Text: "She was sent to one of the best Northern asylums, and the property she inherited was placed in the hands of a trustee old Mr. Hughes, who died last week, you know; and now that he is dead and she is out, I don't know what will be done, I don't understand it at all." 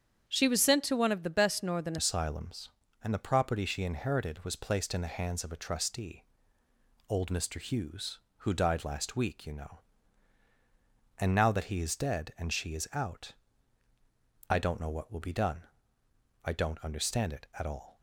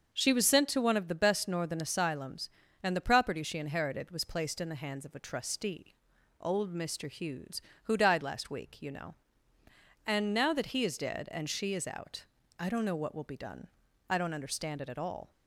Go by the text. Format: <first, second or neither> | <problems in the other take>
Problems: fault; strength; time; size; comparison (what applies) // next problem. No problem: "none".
second | starts louder than the rest; strong; until 1.3 s; 8 dB; also in the second // changes voice at "asylums"; from 1.9 s on; 16.1 s long // pauses between "trustee" and "old"; noticeable; at 6.2 s; 0.84 s long; noticeable in the second